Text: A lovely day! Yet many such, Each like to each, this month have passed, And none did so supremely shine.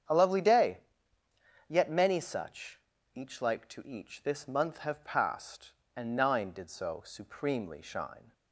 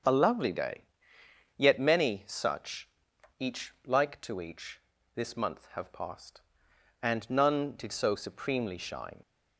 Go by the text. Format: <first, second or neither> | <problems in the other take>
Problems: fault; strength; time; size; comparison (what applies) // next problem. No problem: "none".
second | starts louder than the rest; strong; until 1.9 s; 8 dB; also in the second // says "nine" for "none"; at 6.1 s